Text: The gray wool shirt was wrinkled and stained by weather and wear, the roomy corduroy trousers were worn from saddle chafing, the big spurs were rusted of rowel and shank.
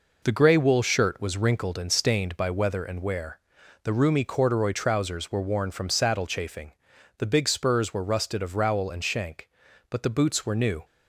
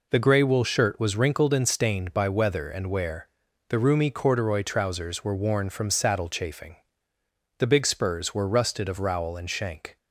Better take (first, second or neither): second